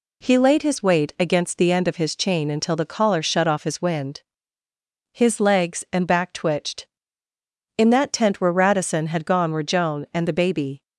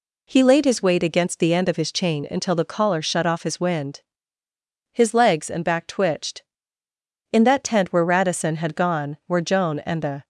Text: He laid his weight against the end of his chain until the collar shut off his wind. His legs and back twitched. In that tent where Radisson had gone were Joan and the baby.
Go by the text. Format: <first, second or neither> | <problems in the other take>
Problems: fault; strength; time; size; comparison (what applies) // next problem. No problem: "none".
first | stops before "baby"; at 10.2 s